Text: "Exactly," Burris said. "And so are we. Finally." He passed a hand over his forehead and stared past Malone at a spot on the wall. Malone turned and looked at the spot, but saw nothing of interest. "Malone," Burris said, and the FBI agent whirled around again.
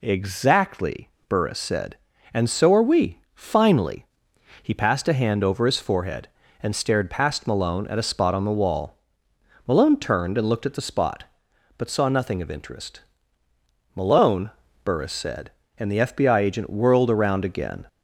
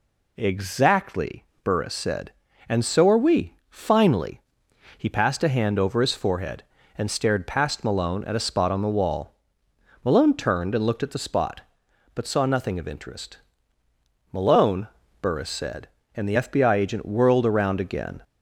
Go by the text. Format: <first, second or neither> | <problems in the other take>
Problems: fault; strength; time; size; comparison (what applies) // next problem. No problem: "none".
neither | none